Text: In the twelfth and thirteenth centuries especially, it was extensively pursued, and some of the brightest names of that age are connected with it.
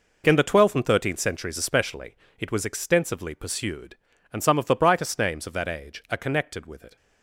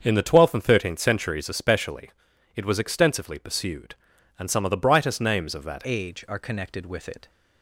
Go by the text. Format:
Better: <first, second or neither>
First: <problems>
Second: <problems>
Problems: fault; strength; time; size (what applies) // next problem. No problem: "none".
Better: first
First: none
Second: starts louder than the rest; until 1.0 s; 6.5 dB // changes voice at "age"; from 5.8 s on; 1.4 s long